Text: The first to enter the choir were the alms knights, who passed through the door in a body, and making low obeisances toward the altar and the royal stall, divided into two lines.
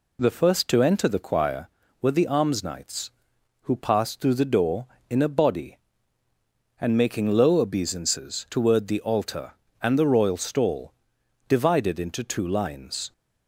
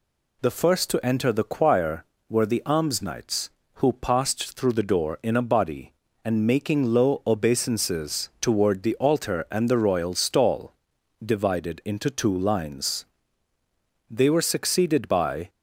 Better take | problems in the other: first | goes on to say "They were succeeded by"; from 14.1 s on; 1.3 s long

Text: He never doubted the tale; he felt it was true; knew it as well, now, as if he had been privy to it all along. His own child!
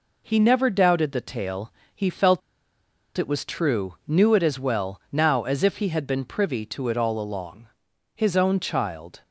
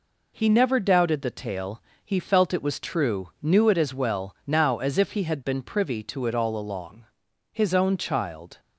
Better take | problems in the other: second | pauses between "felt" and "it"; noticeable; at 2.4 s; 0.77 s long

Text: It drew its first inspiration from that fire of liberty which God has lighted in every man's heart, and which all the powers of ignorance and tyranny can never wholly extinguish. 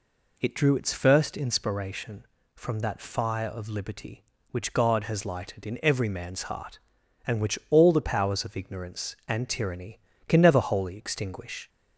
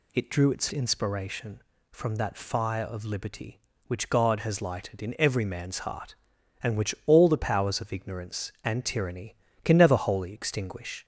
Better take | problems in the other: first | skips "first"; at 0.6 s

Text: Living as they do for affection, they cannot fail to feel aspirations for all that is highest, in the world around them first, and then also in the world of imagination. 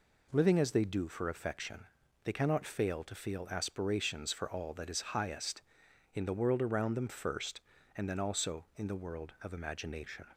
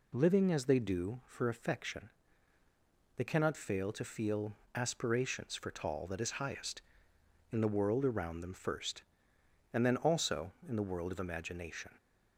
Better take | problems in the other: first | pauses between "feel" and "aspirations"; slight; at 4.5 s; 0.20 s long // says "tall" for "all"; at 5.7 s

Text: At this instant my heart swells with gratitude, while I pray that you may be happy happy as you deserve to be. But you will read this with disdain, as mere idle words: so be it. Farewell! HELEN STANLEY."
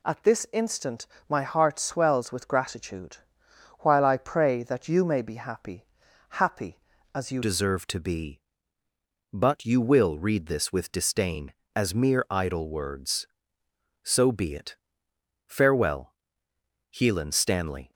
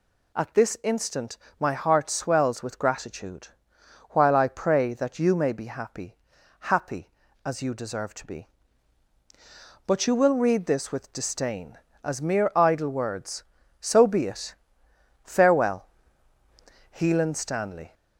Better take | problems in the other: second | pauses between "instant" and "my"; slight; at 1.0 s; 0.22 s long; slight in the second // pauses between "happy" and "happy"; noticeable; at 5.8 s; 0.50 s long; noticeable in the second // changes voice at "deserve"; from 7.4 s on; 10.5 s long

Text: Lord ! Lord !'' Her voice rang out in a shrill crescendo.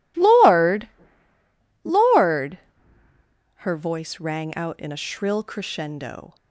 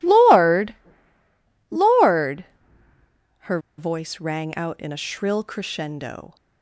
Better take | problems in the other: first | pauses between "Her" and "voice"; slight; at 3.5 s; 0.19 s long

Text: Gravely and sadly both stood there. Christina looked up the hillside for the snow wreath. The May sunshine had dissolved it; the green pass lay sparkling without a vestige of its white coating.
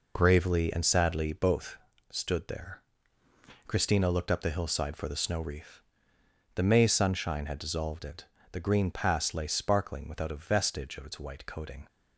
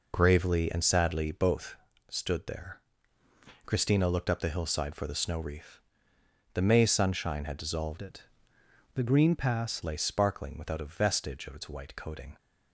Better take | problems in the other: first | pauses between "both" and "stood"; slight; at 1.7 s; 0.34 s long; slight in the first // changes voice from "it" to "pass"; from 8.0 to 9.8 s; 1.8 s long

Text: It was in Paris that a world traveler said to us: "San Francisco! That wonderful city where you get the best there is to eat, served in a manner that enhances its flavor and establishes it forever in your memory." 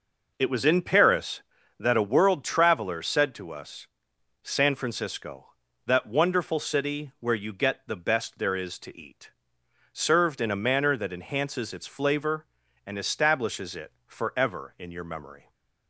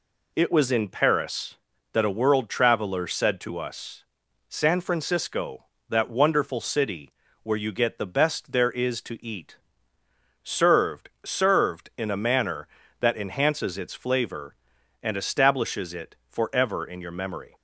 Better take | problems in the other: first | pauses between "city" and "where"; slight; at 7.1 s; 0.30 s long // says "served" twice; at 11.2 s

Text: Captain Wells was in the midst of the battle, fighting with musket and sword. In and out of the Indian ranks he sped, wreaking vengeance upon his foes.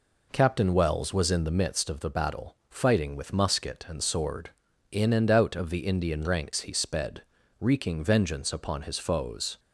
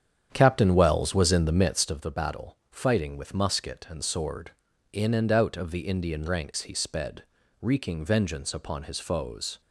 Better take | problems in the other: first | starts louder than the rest; strong; until 2.1 s; 8.5 dB

